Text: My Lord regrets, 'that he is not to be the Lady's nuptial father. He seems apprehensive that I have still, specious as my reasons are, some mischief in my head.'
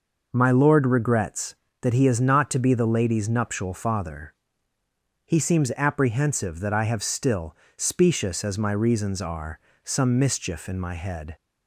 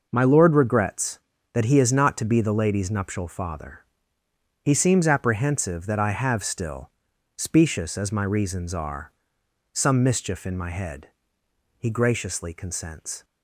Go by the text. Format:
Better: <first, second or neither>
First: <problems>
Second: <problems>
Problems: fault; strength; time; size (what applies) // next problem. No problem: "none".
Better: first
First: none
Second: goes on to say "He graciously consents"; from 11.7 s on; 1.4 s long